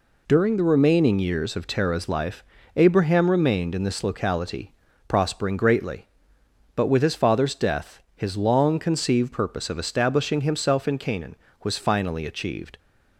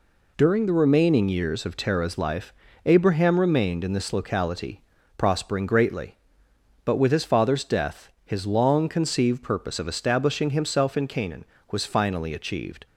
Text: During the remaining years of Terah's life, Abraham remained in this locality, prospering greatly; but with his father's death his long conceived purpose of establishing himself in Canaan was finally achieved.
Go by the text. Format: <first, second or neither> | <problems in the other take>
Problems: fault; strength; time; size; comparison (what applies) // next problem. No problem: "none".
neither | pauses between "death" and "his"; slight; the same in both